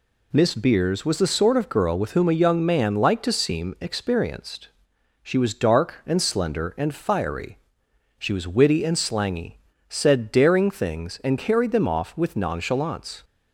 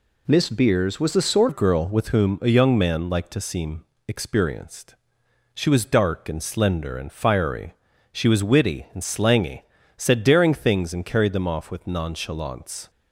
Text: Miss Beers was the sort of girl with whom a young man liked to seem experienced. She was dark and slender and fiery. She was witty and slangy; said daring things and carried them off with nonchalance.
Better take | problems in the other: first | changes voice at "of"; from 1.4 s on; 11.4 s long // pauses between "seem" and "experienced"; slight; at 3.8 s; 0.22 s long

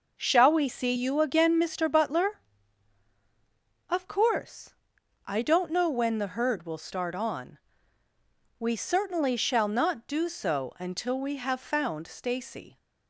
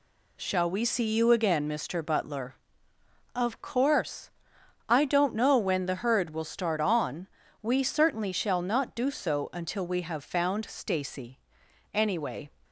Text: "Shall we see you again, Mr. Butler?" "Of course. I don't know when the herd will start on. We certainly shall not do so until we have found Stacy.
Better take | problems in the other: first | goes on to say "Anyway"; from 11.9 s on; 0.58 s long

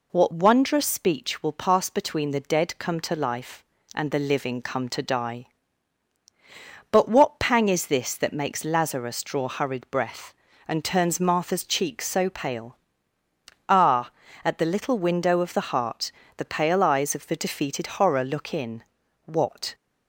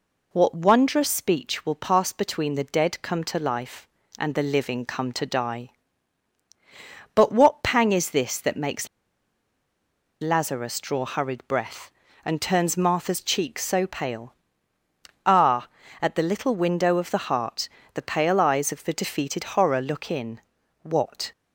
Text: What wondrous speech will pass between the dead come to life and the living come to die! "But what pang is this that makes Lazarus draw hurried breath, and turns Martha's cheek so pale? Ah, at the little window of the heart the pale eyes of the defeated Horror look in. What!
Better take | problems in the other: first | pauses between "makes" and "Lazarus"; strong; at 8.8 s; 1.3 s long // pauses between "heart" and "the"; slight; at 17.6 s; 0.28 s long; slight in the first

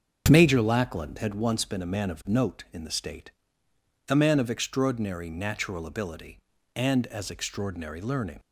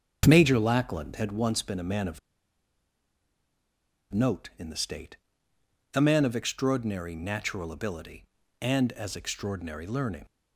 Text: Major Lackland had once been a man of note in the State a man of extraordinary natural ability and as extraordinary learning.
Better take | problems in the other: first | starts louder than the rest; until 1.2 s; 7 dB; also in the first // pauses between "of" and "note"; strong; at 2.1 s; 1.9 s long // pauses between "State" and "a"; noticeable; at 5.1 s; 0.76 s long; noticeable in the first

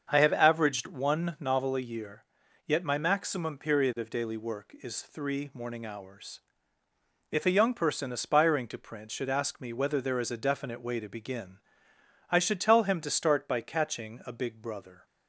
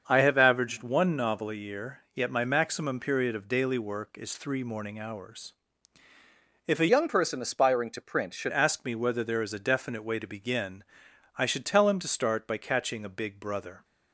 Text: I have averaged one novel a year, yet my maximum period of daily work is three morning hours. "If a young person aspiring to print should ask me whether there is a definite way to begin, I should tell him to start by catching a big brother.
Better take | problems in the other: first | starts louder than the rest; until 1.0 s; 7 dB; also in the first // changes voice from "young" to "should"; from 6.8 to 8.5 s; 1.7 s long

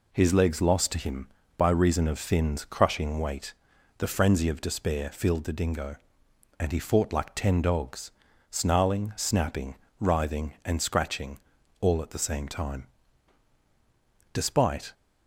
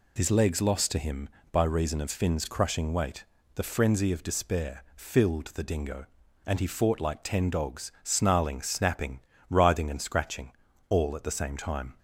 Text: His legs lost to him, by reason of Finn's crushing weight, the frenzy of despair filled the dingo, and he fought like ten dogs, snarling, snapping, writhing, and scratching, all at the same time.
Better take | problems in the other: second | goes on to say "Despite"; from 14.3 s on; 0.60 s long

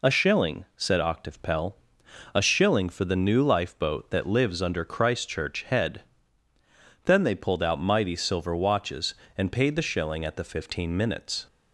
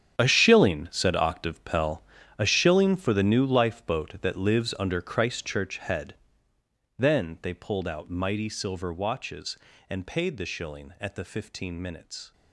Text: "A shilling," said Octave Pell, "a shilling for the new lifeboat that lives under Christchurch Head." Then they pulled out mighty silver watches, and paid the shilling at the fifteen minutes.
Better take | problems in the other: first | gets quieter; strong; throughout; 14.5 dB

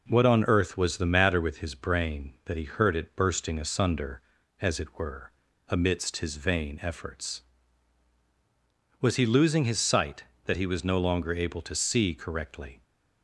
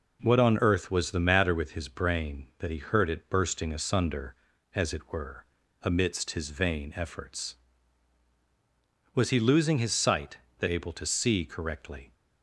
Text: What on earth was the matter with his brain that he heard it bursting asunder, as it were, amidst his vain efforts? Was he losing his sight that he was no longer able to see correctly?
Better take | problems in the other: first | skips "he was no longer"; at 10.6 s

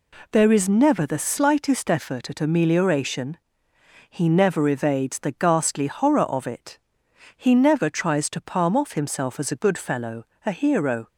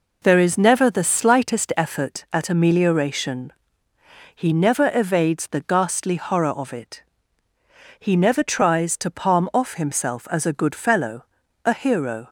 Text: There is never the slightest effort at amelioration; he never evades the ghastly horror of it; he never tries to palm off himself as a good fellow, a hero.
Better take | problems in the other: neither | none

